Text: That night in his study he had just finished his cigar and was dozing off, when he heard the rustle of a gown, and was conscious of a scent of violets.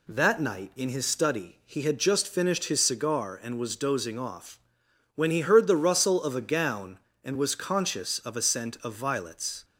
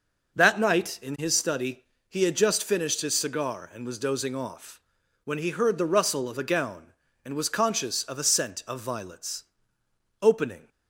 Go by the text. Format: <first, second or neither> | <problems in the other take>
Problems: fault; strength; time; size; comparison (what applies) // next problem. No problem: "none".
first | pauses between "study" and "he"; slight; at 1.8 s; 0.26 s long // goes on to say "Opening"; slight; from 10.2 s on; 0.46 s long